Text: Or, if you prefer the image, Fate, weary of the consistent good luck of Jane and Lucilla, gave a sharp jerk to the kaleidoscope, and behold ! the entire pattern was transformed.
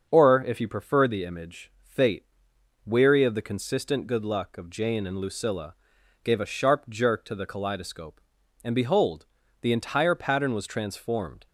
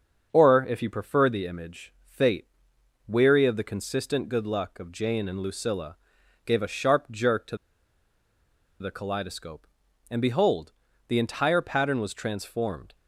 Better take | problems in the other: first | starts louder than the rest; until 1.3 s; 6.5 dB; also in the first // pauses between "to" and "the"; at 7.5 s; 1.2 s long

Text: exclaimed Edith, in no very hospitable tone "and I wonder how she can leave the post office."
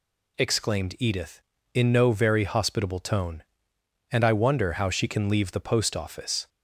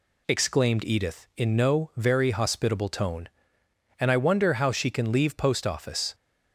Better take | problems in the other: first | skips "the"; at 5.3 s

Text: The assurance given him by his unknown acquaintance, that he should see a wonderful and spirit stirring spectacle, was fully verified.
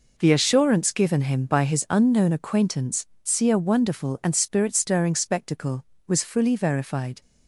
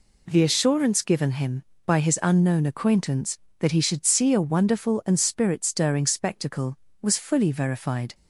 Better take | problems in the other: second | skips "that he should"; at 3.1 s

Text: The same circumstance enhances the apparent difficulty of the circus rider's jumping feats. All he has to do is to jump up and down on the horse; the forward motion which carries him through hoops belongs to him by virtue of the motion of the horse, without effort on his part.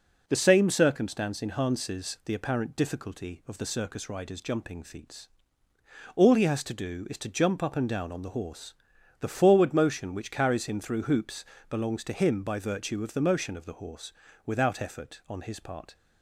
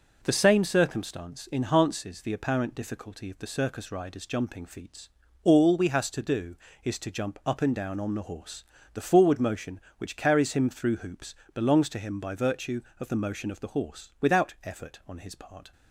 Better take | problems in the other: first | says "we" for "he"; at 5.7 s // pauses between "hoops" and "belongs"; slight; at 11.3 s; 0.22 s long; slight in the first

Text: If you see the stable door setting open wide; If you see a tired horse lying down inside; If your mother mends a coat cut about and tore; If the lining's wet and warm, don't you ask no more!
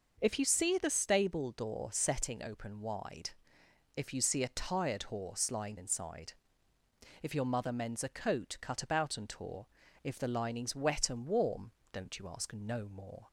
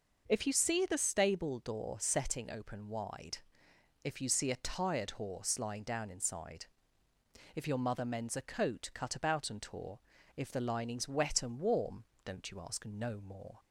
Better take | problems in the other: second | skips "down"; at 5.7 s

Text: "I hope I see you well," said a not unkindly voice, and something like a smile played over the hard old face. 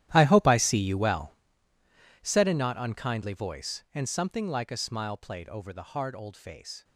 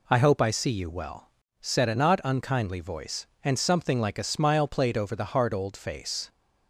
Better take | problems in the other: second | gets quieter; strong; throughout; 17 dB

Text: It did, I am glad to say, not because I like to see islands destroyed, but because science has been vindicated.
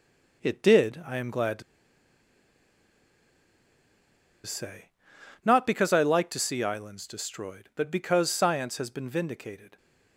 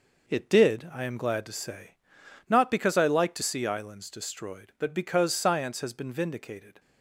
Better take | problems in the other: second | pauses between "to" and "say"; strong; at 1.6 s; 2.8 s long

